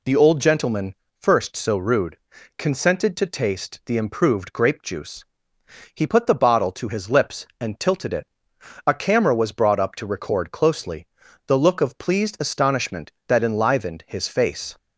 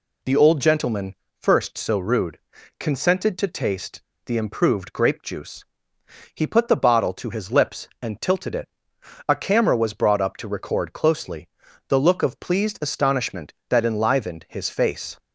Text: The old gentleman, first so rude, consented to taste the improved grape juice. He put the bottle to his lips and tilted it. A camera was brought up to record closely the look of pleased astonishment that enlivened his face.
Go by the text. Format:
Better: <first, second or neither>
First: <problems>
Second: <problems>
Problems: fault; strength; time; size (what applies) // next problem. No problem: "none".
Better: first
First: pauses between "closely" and "the"; at 11.0 s; 0.42 s long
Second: pauses between "taste" and "the"; slight; at 4.0 s; 0.22 s long // pauses between "closely" and "the"; at 11.4 s; 0.42 s long